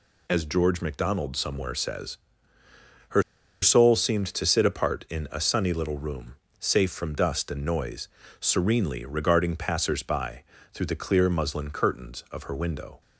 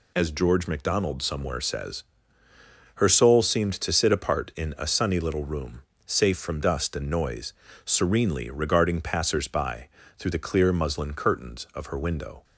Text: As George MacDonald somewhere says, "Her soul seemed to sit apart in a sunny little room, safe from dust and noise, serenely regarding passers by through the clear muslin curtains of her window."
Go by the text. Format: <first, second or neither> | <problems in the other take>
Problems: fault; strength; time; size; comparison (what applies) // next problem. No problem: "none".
second | pauses between "Her" and "soul"; at 3.2 s; 0.39 s long // pauses between "by" and "through"; slight; at 10.4 s; 0.30 s long; slight in the second